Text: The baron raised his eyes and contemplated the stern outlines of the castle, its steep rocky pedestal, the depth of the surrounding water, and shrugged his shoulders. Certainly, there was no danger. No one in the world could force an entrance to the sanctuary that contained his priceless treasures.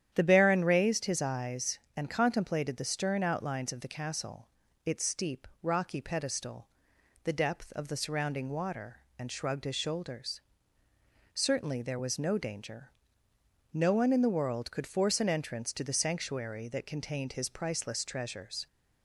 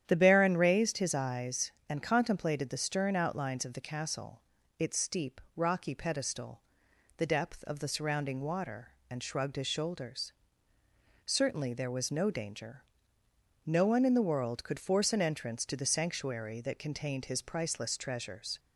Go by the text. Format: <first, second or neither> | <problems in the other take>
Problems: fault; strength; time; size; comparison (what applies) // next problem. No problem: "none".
neither | starts louder than the rest; strong; the same in both // pauses between "steep" and "rocky"; slight; the same in both